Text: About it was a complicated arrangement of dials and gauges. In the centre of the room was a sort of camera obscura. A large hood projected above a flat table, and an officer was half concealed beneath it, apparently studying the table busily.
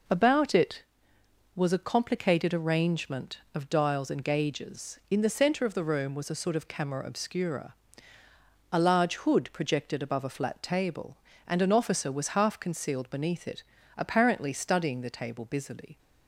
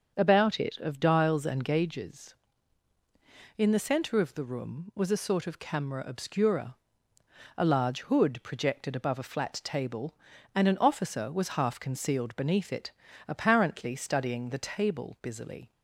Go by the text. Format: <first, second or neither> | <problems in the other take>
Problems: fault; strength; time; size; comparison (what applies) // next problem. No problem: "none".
first | starts louder than the rest; until 1.1 s; 6.5 dB // skips "was a complicated arrangement"; at 0.7 s